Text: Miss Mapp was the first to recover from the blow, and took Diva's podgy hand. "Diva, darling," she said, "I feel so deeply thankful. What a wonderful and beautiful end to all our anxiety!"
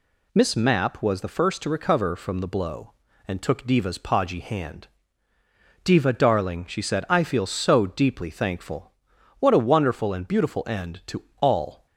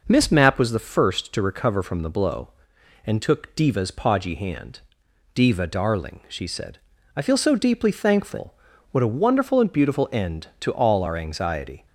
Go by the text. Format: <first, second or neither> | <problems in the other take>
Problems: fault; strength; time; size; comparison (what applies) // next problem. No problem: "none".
second | pauses between "to" and "all"; slight; at 11.2 s; 0.16 s long // stops before "our anxiety"; at 11.8 s